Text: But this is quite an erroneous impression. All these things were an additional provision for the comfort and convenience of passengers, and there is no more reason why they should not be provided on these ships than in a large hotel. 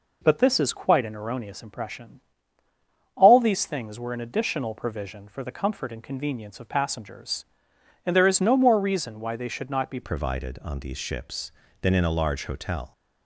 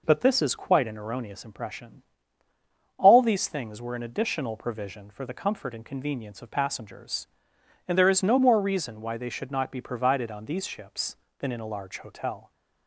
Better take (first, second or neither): second